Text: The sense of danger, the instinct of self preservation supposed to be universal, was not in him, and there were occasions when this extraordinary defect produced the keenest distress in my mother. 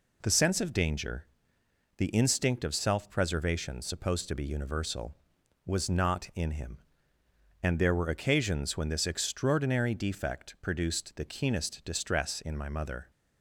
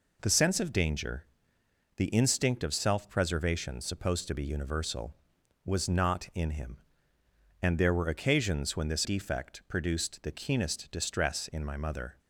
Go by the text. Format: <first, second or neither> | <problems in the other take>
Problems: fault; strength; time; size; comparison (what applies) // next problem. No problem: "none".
first | skips "extraordinary"; at 9.0 s